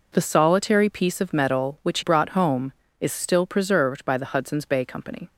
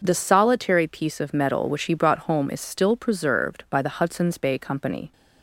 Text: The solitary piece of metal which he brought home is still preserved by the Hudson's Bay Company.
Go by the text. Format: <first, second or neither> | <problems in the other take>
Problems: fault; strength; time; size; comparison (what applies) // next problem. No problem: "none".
second | skips "he"; at 2.0 s